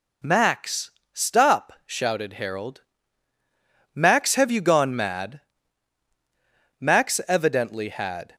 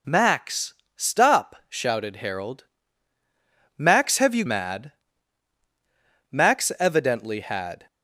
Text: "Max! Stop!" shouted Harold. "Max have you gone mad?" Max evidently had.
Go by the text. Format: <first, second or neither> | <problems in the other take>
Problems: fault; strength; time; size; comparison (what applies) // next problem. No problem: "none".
first | skips "gone"; at 4.4 s